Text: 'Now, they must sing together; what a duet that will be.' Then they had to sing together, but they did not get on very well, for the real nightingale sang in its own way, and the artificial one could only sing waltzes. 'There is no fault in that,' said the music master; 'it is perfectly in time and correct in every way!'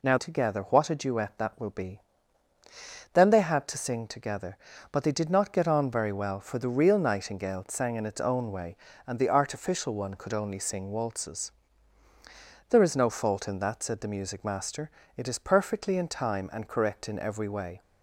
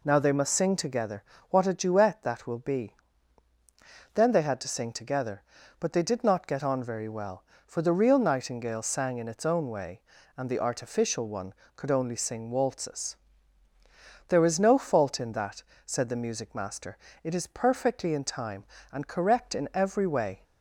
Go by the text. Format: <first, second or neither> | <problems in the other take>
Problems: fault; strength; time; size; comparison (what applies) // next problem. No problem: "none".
second | skips "they must sing"; at 0.1 s